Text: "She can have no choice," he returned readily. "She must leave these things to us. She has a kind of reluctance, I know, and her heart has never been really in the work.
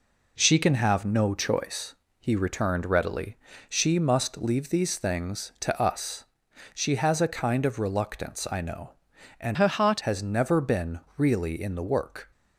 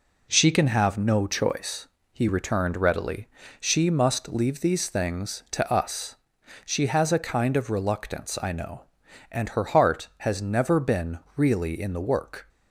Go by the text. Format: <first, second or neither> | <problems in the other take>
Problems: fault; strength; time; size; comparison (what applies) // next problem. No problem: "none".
second | changes voice from "her" to "heart"; from 9.5 to 10.0 s; 0.5 s long // pauses between "been" and "really"; slight; at 11.0 s; 0.18 s long; slight in the second